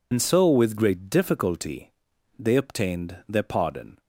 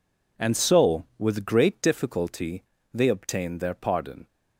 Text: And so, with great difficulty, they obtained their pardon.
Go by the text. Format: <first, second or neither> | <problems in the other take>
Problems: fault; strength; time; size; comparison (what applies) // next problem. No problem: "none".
second | loses the start of "And"; at 0.1 s; 85 ms